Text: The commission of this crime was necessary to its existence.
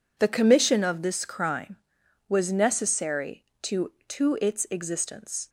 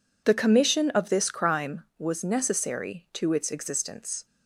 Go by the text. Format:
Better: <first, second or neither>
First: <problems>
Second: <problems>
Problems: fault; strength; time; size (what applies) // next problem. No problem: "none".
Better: second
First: says "to" twice; at 4.0 s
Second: none